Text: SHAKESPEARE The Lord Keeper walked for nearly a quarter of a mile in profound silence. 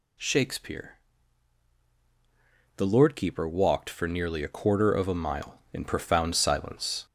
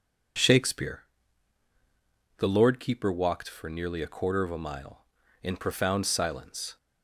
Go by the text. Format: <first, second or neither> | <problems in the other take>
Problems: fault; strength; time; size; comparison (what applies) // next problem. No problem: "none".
second | gets louder; throughout; 3.5 dB // pauses between "SHAKESPEARE" and "The"; strong; at 0.9 s; 1.8 s long; strong in the second